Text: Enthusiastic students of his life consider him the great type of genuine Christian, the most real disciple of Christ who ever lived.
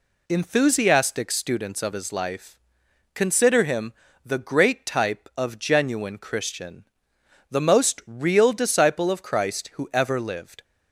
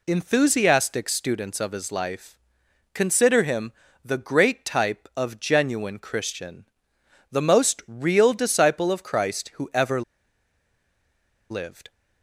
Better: first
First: pauses between "life" and "consider"; noticeable; at 2.5 s; 0.54 s long // pauses between "him" and "the"; slight; at 3.9 s; 0.32 s long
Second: pauses between "life" and "consider"; noticeable; at 2.3 s; 0.54 s long // pauses between "him" and "the"; slight; at 3.7 s; 0.32 s long // pauses between "ever" and "lived"; strong; at 10.0 s; 1.4 s long

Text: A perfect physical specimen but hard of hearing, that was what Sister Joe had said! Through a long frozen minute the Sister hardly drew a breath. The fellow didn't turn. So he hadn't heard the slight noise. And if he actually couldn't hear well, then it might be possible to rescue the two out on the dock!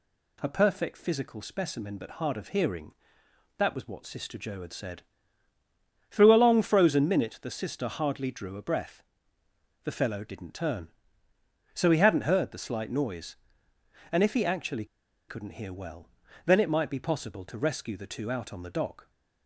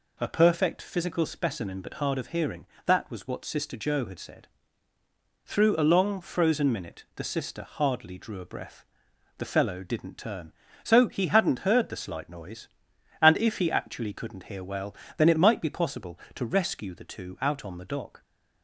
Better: second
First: pauses between "actually" and "couldn't"; at 14.8 s; 0.43 s long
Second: none

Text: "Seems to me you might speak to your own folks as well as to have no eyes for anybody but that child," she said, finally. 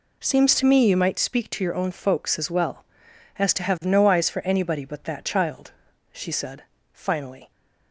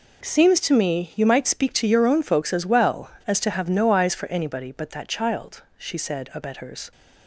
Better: first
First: none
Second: says "abettors" for "finally"; at 6.3 s

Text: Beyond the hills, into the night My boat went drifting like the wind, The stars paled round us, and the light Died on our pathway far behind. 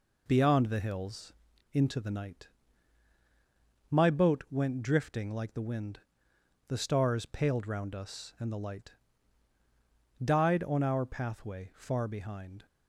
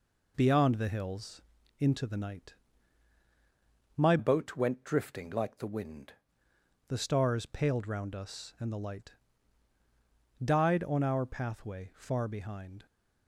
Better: first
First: pauses between "night" and "My"; strong; at 2.4 s; 1.4 s long // pauses between "light" and "Died"; strong; at 8.9 s; 1.3 s long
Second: pauses between "night" and "My"; strong; at 2.5 s; 1.4 s long // changes voice from "boat" to "wind"; from 4.1 to 6.1 s; 2.0 s long // pauses between "light" and "Died"; strong; at 9.1 s; 1.3 s long

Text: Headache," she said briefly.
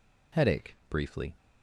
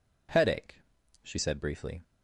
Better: second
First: skips "she said"; at 0.8 s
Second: none

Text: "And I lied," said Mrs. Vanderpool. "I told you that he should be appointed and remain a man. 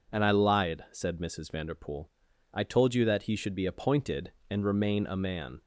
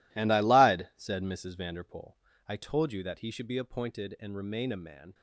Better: first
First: none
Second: gets quieter; strong; throughout; 12.5 dB

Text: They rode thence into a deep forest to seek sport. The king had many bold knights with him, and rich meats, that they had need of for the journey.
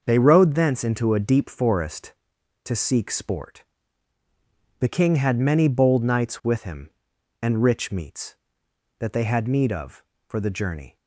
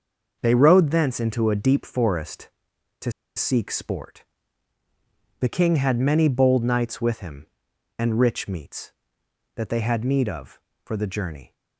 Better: first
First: starts louder than the rest; until 1.0 s; 6.5 dB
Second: starts louder than the rest; until 1.4 s; 6 dB // pauses between "to" and "seek"; slight; at 3.1 s; 0.26 s long

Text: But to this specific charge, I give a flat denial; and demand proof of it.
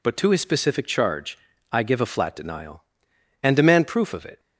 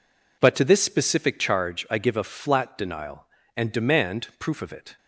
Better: second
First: says "his" for "this"; at 0.3 s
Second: none

